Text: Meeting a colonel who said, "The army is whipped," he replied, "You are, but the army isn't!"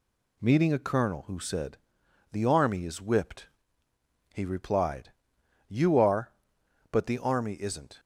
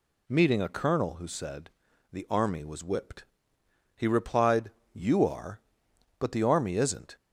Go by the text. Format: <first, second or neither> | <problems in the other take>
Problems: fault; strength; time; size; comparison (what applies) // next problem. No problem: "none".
first | says "was" for "is"; at 2.6 s